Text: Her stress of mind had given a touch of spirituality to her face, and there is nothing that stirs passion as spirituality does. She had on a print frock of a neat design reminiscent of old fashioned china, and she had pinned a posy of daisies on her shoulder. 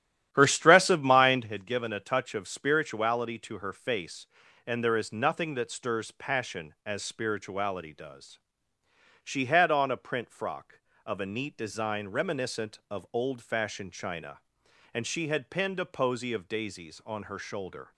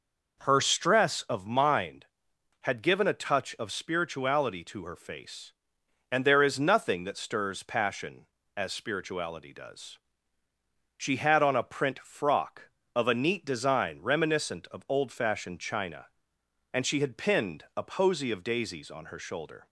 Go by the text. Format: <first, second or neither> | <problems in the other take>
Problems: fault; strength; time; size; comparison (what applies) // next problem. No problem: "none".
second | starts louder than the rest; strong; until 1.6 s; 11 dB